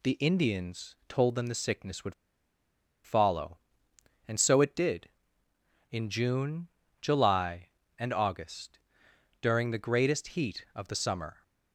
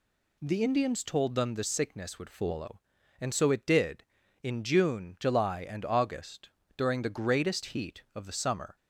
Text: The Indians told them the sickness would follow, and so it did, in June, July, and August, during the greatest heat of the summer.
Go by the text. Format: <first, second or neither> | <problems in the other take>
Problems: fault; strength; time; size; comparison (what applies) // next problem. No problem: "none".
second | pauses between "would" and "follow"; noticeable; at 2.1 s; 0.90 s long